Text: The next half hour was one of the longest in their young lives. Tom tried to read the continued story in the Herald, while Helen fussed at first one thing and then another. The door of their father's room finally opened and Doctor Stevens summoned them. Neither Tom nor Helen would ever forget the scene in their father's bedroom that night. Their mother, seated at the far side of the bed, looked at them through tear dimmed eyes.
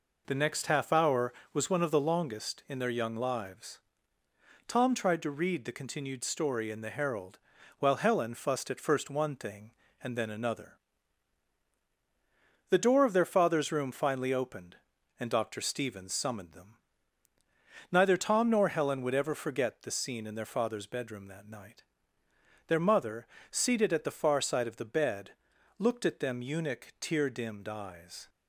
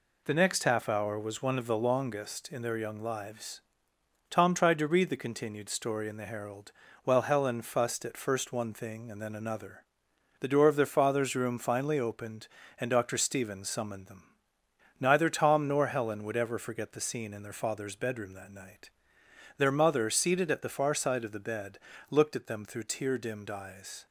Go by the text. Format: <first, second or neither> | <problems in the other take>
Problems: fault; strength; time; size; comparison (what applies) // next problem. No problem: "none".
second | says "eunuch" for "through"; at 26.4 s